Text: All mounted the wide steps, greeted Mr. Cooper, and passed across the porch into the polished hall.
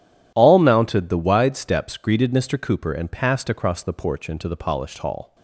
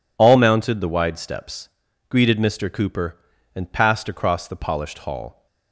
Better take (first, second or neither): first